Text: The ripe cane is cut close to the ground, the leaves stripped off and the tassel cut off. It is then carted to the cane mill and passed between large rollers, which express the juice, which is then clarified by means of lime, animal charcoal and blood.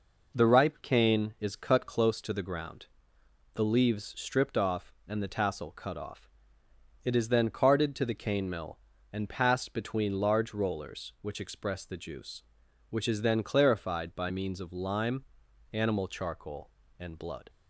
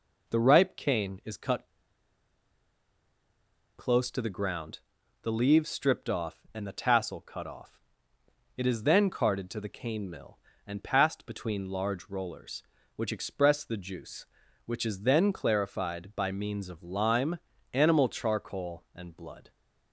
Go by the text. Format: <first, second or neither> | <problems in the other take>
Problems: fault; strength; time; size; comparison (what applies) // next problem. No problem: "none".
first | pauses between "cut" and "close"; strong; at 1.6 s; 2.0 s long